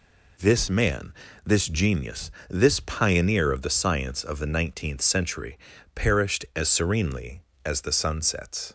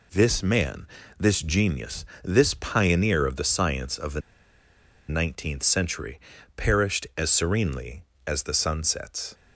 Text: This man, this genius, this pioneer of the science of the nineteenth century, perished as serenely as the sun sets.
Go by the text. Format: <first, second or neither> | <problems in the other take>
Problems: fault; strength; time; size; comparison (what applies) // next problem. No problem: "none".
first | pauses between "the" and "nineteenth"; noticeable; at 4.2 s; 0.88 s long